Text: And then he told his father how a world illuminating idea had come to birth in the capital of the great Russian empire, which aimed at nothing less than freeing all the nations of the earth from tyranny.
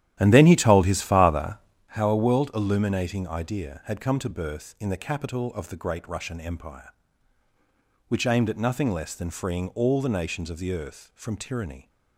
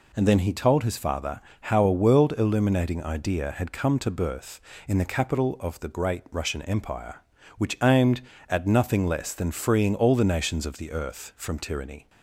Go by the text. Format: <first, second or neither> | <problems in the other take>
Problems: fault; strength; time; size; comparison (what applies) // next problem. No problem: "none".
second | starts louder than the rest; strong; until 1.9 s; 12 dB // pauses between "father" and "how"; slight; at 1.5 s; 0.30 s long; slight in the second